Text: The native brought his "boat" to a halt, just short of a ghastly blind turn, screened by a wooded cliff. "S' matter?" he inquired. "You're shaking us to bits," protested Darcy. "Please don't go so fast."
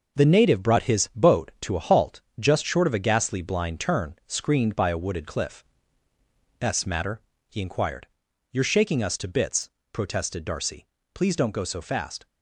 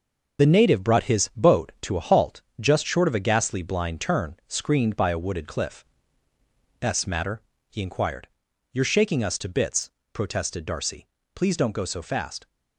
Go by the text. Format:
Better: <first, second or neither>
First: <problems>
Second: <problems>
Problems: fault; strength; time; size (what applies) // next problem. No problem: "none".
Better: first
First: none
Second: loses the start of "The"; at 0.3 s; 30 ms